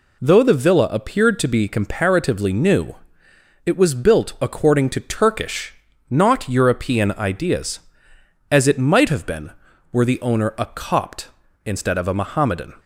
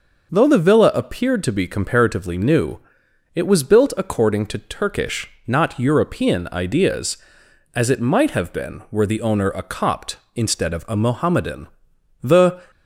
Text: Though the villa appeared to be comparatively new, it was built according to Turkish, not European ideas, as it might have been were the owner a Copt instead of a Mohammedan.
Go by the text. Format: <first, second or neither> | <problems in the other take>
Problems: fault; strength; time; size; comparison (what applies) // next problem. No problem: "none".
first | goes on to say "The"; slight; from 12.2 s on; 0.48 s long